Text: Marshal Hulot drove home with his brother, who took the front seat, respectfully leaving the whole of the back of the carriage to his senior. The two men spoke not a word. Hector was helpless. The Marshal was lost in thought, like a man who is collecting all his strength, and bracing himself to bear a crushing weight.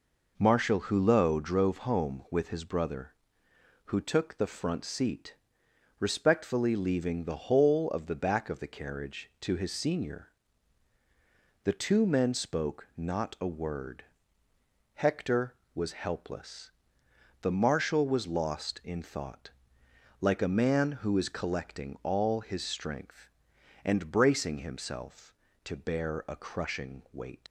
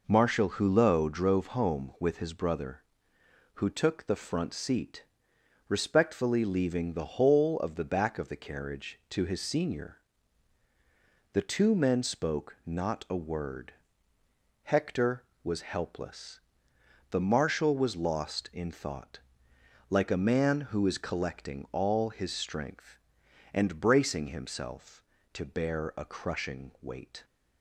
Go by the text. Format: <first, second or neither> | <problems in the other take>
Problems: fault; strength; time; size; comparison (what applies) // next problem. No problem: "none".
second | leaves "weight" unfinished; at 27.4 s; 90 ms